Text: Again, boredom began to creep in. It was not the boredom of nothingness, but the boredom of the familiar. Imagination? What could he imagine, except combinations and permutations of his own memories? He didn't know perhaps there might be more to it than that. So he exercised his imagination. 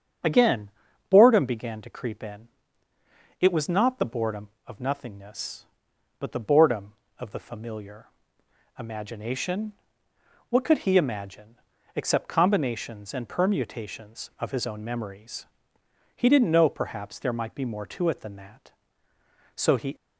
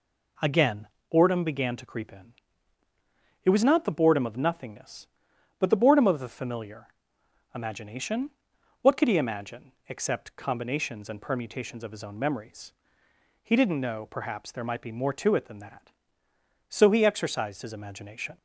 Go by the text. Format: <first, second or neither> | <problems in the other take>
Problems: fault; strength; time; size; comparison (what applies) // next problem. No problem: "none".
second | starts louder than the rest; strong; until 1.6 s; 8 dB // stops before "exercised his imagination"; at 19.9 s